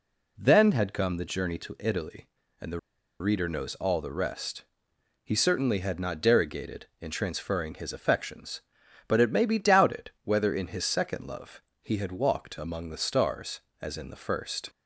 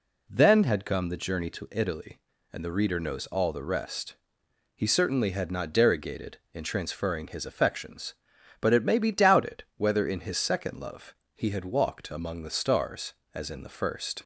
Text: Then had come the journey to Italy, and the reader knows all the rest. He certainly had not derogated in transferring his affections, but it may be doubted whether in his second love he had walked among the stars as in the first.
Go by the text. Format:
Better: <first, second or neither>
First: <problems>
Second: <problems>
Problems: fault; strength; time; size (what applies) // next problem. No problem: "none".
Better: second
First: pauses between "the" and "reader"; at 2.7 s; 0.40 s long // pauses between "love" and "he"; slight; at 11.6 s; 0.20 s long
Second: pauses between "love" and "he"; slight; at 11.1 s; 0.20 s long